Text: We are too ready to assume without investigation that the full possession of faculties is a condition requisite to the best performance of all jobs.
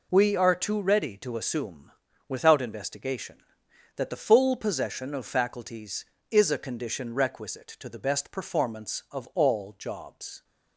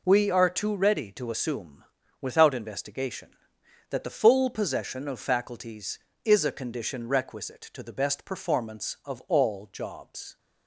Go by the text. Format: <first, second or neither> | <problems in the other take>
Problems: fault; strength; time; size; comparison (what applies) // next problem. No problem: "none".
neither | pauses between "assume" and "without"; slight; the same in both